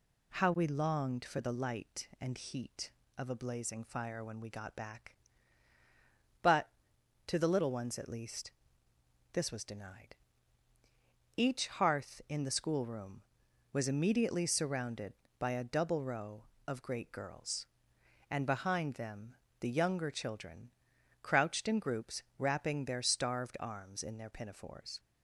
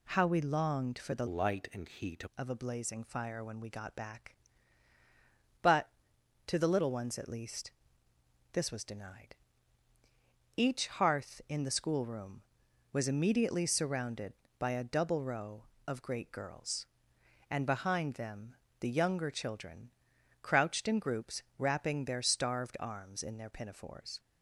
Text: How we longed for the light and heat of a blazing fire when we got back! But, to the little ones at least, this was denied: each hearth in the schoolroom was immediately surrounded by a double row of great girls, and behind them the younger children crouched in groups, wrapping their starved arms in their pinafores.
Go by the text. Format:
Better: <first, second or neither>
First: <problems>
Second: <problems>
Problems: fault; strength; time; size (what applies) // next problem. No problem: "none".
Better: first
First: pauses between "them" and "the"; slight; at 19.3 s; 0.24 s long // pauses between "children" and "crouched"; noticeable; at 20.6 s; 0.52 s long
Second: changes voice from "light" to "heat"; from 1.2 to 2.2 s; 1.0 s long // pauses between "them" and "the"; slight; at 18.5 s; 0.24 s long // pauses between "children" and "crouched"; noticeable; at 19.8 s; 0.52 s long